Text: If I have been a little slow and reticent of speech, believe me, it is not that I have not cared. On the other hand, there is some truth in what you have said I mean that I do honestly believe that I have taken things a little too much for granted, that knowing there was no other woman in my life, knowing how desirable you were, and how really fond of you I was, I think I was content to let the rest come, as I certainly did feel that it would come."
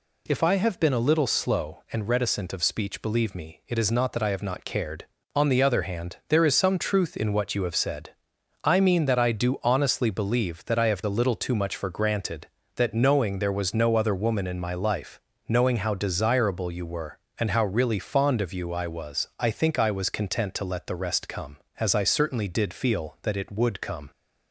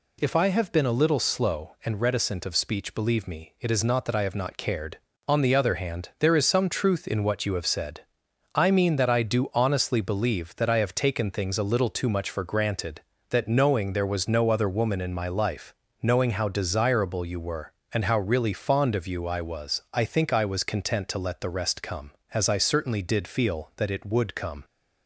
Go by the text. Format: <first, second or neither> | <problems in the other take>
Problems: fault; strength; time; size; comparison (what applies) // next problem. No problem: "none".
second | pauses between "said" and "I"; noticeable; at 8.0 s; 0.56 s long; noticeable in the second // skips "taken things"; at 11.0 s